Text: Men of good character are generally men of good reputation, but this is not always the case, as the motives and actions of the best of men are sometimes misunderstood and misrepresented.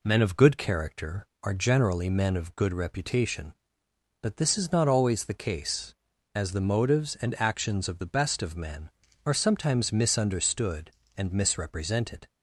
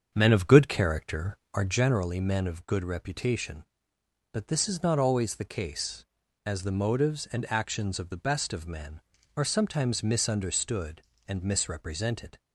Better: first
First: none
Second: starts louder than the rest; strong; until 1.9 s; 7 dB

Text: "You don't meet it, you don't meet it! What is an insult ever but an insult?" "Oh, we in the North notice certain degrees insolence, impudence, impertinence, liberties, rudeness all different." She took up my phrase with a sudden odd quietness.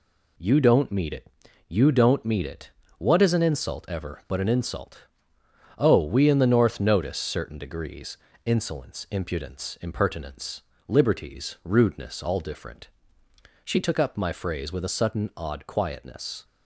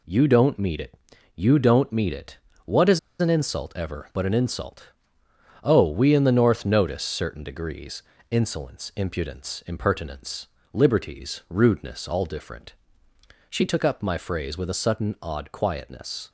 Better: first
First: pauses between "degrees" and "insolence"; slight; at 8.1 s; 0.26 s long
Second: pauses between "is" and "an"; slight; at 2.9 s; 0.21 s long // pauses between "degrees" and "insolence"; slight; at 8.0 s; 0.26 s long

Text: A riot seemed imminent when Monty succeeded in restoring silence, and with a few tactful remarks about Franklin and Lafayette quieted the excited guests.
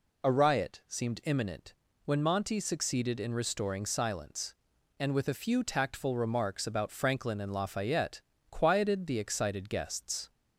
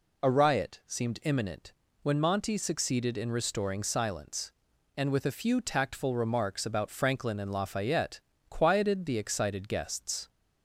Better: neither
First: pauses between "imminent" and "when"; slight; at 1.7 s; 0.30 s long // pauses between "Lafayette" and "quieted"; slight; at 8.2 s; 0.28 s long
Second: pauses between "imminent" and "when"; slight; at 1.7 s; 0.28 s long // pauses between "Lafayette" and "quieted"; slight; at 8.2 s; 0.28 s long

